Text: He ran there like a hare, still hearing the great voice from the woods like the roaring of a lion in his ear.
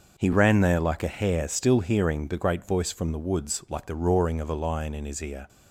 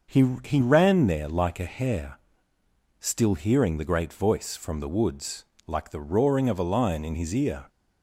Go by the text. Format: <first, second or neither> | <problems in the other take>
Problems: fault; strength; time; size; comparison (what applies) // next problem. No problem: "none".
first | starts louder than the rest; noticeable; until 1.2 s; 6 dB; noticeable in the first // says "He" twice; at 0.4 s // pauses between "woods" and "like"; slight; at 5.4 s; 0.22 s long